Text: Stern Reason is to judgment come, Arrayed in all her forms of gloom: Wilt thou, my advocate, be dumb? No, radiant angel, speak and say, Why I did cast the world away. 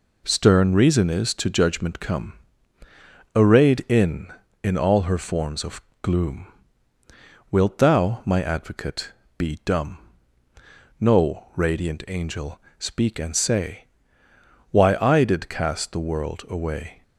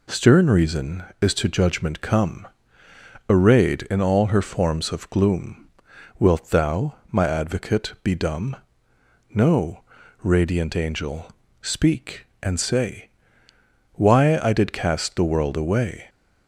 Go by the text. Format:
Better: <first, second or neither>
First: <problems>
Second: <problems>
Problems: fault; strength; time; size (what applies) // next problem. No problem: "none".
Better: second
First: says "in" twice; at 4.6 s // pauses between "of" and "gloom"; slight; at 5.8 s; 0.18 s long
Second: none